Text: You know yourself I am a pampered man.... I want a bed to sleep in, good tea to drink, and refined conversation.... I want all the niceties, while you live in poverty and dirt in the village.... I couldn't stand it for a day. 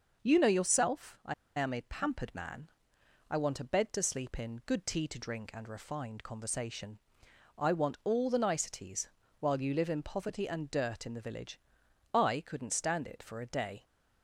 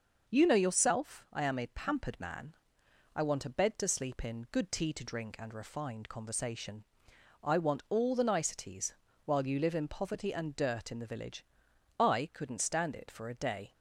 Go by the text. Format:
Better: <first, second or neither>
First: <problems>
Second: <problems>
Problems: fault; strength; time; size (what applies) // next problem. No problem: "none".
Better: second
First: starts louder than the rest; noticeable; until 1.2 s; 6 dB // pauses between "I" and "am"; slight; at 1.3 s; 0.24 s long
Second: starts louder than the rest; noticeable; until 1.3 s; 6 dB